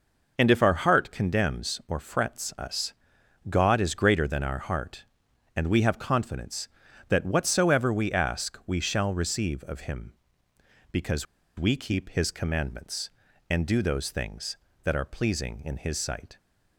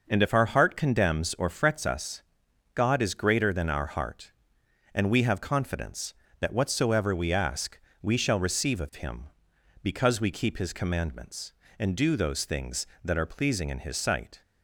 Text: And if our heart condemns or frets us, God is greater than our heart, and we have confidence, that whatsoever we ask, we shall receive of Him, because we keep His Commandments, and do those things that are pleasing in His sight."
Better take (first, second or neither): second